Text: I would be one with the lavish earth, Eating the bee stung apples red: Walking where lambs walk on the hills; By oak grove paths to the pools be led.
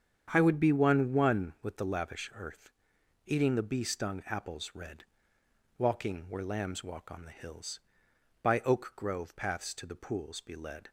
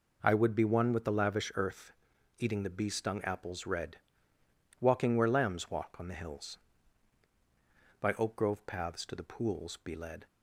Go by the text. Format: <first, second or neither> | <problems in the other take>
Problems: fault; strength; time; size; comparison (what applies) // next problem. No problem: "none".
second | starts louder than the rest; strong; until 1.3 s; 8 dB // says "one" twice; at 1.1 s